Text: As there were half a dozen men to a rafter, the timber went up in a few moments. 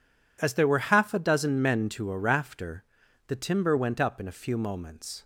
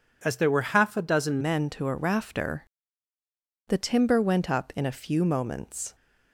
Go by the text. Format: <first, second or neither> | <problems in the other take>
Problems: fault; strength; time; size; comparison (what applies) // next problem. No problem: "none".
first | changes voice at "men"; from 1.4 s on; 4.5 s long